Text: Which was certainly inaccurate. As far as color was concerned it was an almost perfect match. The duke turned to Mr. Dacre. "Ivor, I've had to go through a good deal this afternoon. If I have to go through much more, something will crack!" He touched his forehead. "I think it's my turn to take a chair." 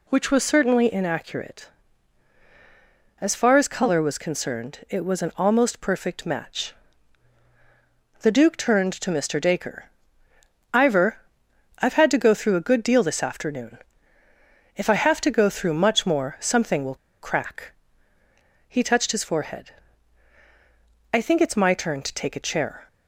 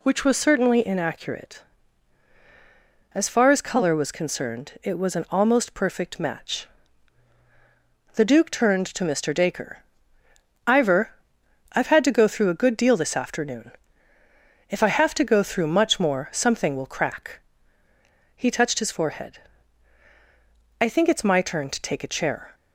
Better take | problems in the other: second | pauses between "will" and "crack"; slight; at 16.9 s; 0.26 s long

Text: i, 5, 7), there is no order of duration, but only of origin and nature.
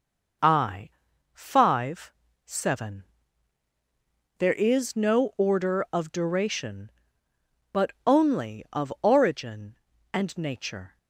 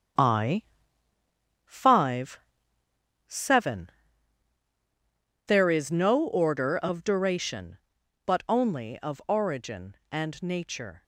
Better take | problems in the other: first | gets quieter; strong; throughout; 10 dB

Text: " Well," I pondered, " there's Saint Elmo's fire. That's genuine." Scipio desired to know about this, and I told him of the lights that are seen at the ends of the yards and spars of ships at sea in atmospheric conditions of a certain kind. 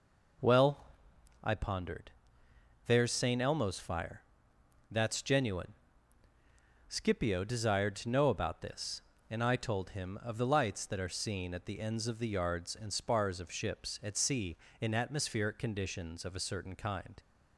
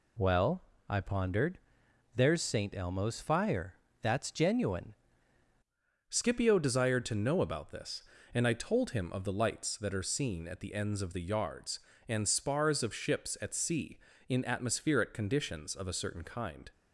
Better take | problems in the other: first | changes voice at "Scipio"; from 6.0 s on; 10.7 s long

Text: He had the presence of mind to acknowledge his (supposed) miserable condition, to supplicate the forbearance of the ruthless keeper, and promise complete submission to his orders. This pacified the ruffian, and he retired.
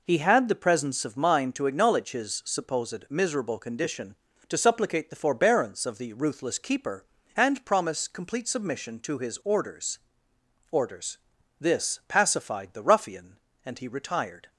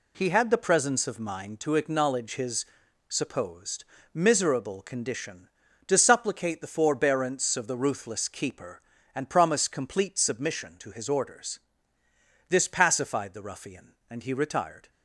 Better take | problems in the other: second | says "orders" twice; at 10.6 s

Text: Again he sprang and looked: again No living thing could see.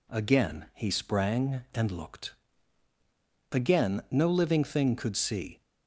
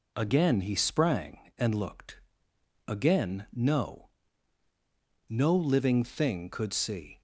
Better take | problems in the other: first | says "No" twice; at 5.2 s

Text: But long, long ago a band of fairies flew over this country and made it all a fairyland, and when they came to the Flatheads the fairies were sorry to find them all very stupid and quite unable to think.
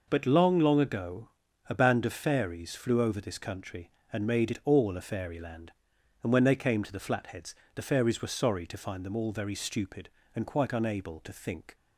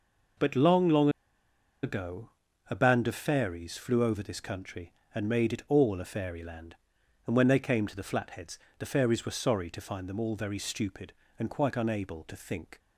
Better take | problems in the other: first | pauses between "long" and "ago"; noticeable; at 1.0 s; 0.73 s long // pauses between "ago" and "a"; at 2.3 s; 0.40 s long; also in the first // pauses between "Flatheads" and "the"; slight; at 8.5 s; 0.18 s long; slight in the first

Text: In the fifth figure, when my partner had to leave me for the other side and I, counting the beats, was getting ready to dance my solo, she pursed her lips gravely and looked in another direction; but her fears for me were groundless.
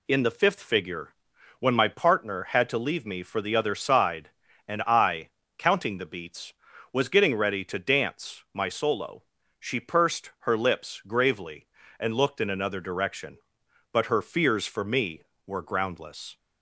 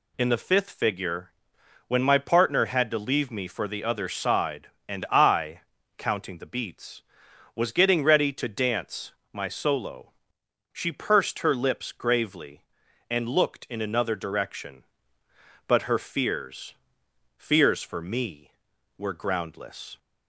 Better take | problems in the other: first | pauses between "dance" and "my"; slight; at 9.1 s; 0.20 s long // says "fears" twice; at 17.3 s

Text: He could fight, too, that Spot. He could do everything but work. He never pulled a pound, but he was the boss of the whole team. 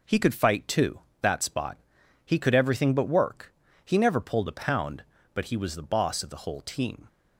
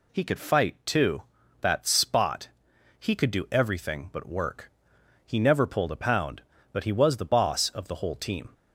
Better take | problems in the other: second | skips "do"; at 2.5 s

